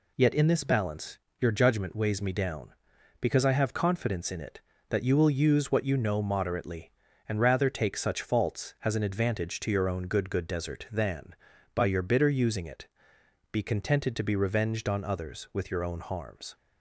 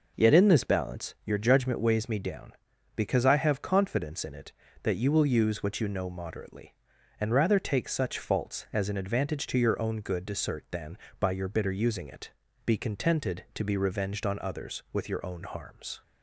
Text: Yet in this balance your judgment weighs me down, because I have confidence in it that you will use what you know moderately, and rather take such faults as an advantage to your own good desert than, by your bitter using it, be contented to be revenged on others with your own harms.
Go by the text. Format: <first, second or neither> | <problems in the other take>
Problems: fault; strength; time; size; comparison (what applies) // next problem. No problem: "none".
second | pauses between "balance" and "your"; slight; at 1.1 s; 0.22 s long // says "good" twice; at 10.2 s